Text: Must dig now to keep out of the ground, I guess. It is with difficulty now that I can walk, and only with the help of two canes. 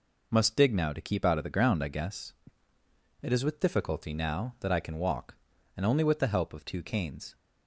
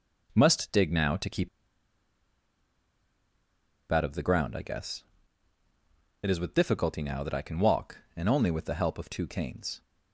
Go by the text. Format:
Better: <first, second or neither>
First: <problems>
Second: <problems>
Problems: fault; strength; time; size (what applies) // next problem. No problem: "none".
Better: first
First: none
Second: pauses between "keep" and "out"; strong; at 1.4 s; 2.4 s long